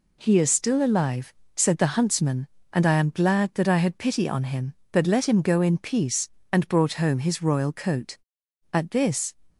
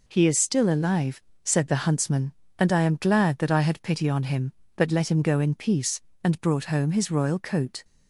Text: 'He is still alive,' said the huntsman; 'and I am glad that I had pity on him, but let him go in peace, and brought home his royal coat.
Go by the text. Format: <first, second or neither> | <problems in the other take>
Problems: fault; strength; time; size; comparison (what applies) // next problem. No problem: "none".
second | goes on to say "At this"; from 8.7 s on; 0.60 s long